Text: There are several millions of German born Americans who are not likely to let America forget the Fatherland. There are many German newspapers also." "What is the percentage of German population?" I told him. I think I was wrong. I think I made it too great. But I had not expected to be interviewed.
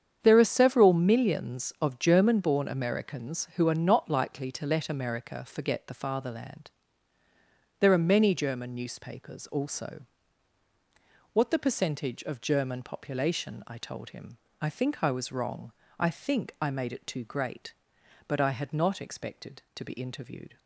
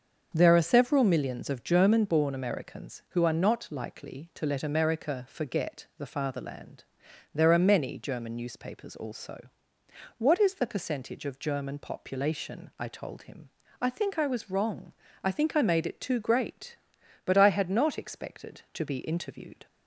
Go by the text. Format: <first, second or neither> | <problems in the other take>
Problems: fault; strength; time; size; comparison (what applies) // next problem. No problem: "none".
second | starts louder than the rest; strong; until 1.2 s; 8 dB; also in the second // skips "is"; at 11.5 s